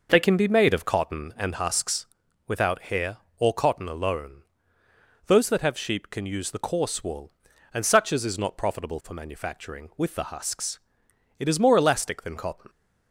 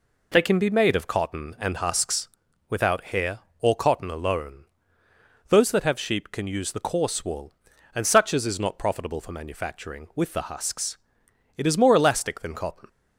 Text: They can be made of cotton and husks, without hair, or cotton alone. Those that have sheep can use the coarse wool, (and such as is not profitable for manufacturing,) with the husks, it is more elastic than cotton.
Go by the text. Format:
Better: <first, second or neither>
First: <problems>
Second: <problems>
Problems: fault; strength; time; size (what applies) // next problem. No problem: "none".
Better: second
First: starts louder than the rest; noticeable; until 1.4 s; 5.5 dB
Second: none